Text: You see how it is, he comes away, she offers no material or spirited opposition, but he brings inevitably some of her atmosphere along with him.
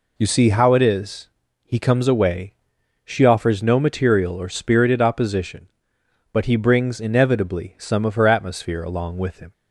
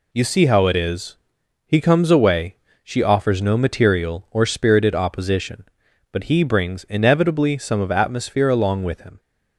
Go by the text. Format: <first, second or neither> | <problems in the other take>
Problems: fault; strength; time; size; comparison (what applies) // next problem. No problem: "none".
first | skips "her"; at 7.9 s